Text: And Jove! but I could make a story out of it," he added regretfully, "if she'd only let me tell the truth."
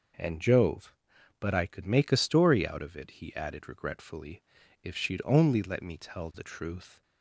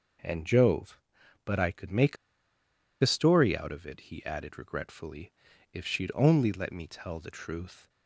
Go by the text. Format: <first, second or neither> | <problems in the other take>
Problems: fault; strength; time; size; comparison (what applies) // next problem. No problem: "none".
first | pauses between "make" and "a"; noticeable; at 2.1 s; 0.84 s long